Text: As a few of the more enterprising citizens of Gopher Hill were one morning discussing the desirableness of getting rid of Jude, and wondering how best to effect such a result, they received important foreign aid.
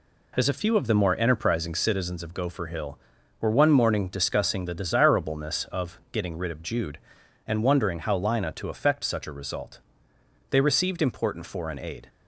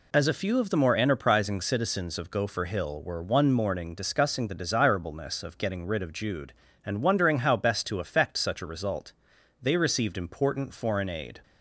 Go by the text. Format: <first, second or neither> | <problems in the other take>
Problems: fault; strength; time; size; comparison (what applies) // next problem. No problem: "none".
second | says "lina" for "best"; at 8.1 s